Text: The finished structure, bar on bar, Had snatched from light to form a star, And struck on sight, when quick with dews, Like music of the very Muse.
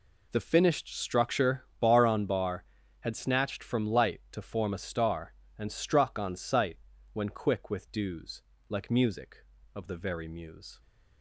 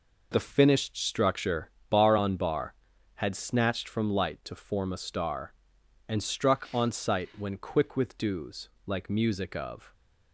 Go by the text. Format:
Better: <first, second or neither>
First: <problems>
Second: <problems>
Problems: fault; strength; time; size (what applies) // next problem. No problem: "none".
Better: first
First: none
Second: stops before "the very Muse"; at 9.9 s